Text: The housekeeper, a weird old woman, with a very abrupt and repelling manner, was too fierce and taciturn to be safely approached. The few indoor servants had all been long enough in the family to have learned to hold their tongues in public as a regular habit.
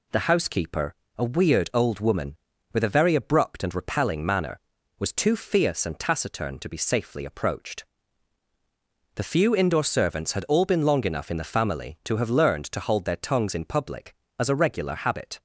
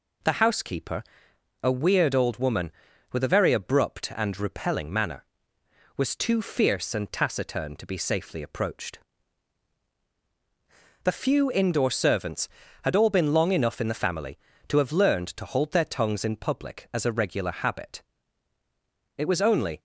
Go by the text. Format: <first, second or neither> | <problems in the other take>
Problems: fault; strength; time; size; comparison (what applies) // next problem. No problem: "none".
first | goes on to say "It was only"; noticeable; from 19.1 s on; 0.64 s long